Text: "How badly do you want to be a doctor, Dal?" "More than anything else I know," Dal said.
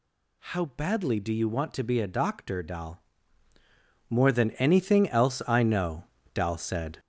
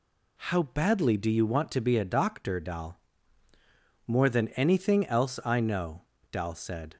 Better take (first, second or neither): second